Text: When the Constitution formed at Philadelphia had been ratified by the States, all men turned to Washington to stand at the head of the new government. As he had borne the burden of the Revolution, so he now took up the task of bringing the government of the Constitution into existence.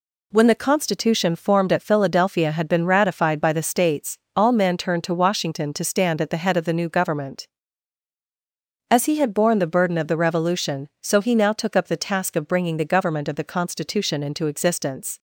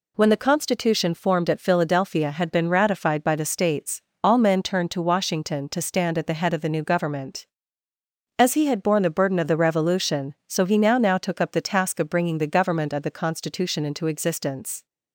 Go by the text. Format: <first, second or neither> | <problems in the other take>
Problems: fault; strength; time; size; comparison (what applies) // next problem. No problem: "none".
first | says "now" twice; at 10.9 s